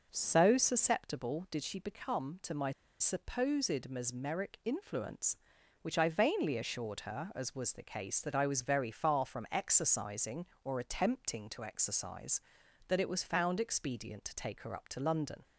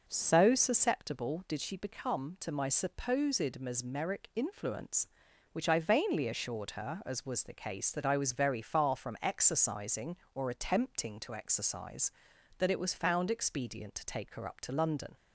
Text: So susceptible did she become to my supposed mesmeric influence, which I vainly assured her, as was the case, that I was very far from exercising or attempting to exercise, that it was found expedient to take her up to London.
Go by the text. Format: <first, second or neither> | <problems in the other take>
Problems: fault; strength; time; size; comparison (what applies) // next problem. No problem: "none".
second | starts louder than the rest; noticeable; until 1.1 s; 6 dB // pauses between "my" and "supposed"; slight; at 2.7 s; 0.27 s long